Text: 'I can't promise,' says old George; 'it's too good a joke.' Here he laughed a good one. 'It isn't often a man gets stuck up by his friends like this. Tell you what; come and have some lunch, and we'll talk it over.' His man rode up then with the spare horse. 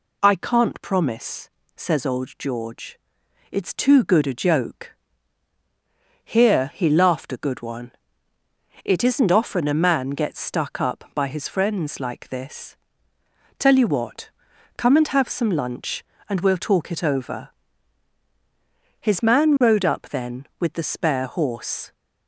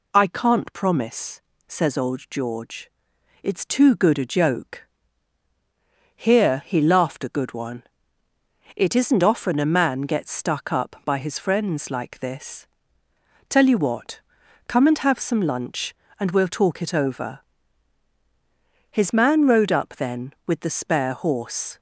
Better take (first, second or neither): neither